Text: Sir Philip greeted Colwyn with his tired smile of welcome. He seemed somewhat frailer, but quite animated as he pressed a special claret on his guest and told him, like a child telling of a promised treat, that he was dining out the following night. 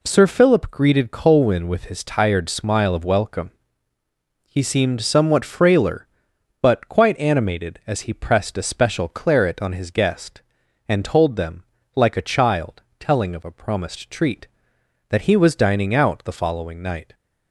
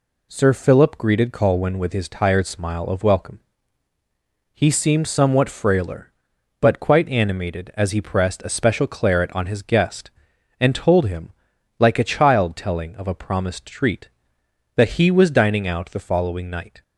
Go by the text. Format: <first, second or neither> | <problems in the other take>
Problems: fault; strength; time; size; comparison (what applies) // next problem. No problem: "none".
second | says "them" for "him"; at 11.3 s // pauses between "child" and "telling"; slight; at 12.8 s; 0.18 s long